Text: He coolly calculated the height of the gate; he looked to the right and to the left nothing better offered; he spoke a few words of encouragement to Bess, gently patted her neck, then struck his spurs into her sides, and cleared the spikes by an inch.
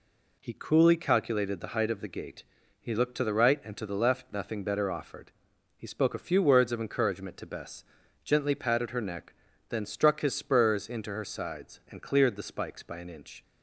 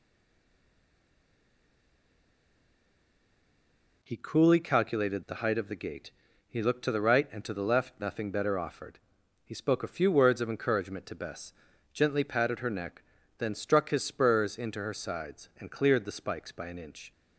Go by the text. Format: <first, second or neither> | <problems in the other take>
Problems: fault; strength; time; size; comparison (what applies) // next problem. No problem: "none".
first | stays silent before the first word; strong; until 4.0 s; 4.0 s long